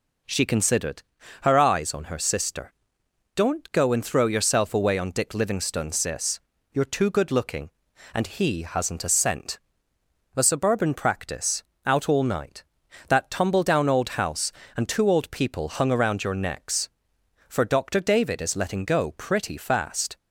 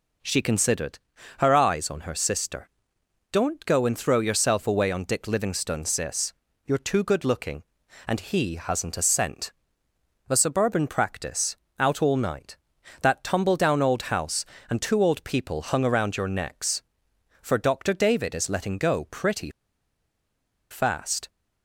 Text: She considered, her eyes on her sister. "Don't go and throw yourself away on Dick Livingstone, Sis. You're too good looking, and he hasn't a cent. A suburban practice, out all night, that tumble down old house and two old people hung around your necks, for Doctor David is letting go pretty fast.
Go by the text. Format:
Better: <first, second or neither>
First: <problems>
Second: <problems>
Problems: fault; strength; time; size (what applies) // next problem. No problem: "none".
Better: first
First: none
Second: pauses between "pretty" and "fast"; at 19.4 s; 1.2 s long